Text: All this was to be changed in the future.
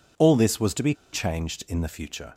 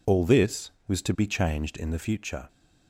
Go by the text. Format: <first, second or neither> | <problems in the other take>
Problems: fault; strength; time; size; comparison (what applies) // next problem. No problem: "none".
second | pauses between "be" and "changed"; slight; at 0.9 s; 0.19 s long